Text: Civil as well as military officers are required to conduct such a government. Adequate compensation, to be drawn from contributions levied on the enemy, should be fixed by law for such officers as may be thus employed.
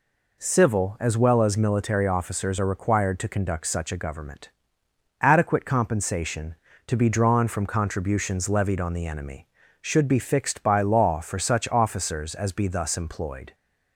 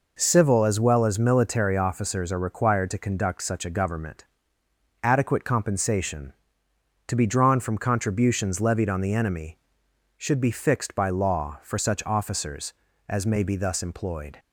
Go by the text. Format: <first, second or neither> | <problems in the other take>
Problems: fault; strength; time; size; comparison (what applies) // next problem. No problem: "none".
second | skips "may"; at 12.5 s